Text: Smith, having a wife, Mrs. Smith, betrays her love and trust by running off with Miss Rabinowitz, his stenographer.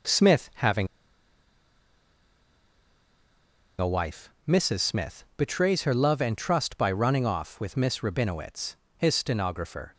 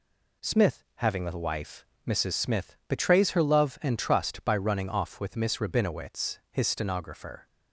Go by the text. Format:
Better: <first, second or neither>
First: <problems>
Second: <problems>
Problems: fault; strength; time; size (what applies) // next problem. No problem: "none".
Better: second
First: pauses between "having" and "a"; strong; at 0.8 s; 2.9 s long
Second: none